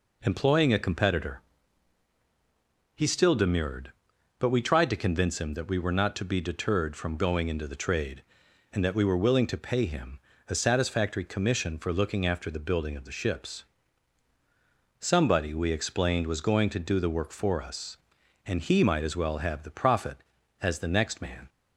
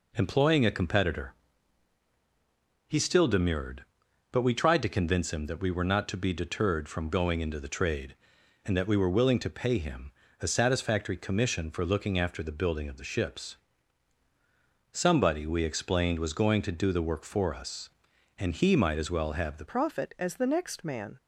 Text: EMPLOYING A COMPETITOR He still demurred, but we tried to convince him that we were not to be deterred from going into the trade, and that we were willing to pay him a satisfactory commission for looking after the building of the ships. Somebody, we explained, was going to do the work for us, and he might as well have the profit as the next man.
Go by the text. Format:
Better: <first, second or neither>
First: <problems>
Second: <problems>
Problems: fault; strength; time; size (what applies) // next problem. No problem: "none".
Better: first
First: pauses between "COMPETITOR" and "He"; strong; at 1.4 s; 1.5 s long // pauses between "him" and "a"; slight; at 10.1 s; 0.30 s long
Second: pauses between "COMPETITOR" and "He"; strong; at 1.3 s; 1.5 s long // pauses between "him" and "a"; slight; at 10.1 s; 0.30 s long // changes voice at "profit"; from 19.6 s on; 1.5 s long